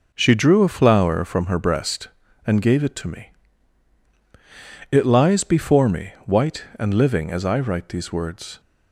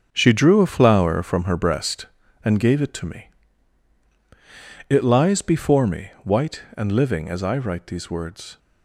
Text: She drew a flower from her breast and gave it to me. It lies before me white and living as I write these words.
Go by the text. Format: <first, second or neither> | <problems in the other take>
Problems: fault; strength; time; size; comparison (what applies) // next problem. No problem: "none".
first | gets quieter; strong; throughout; 9.5 dB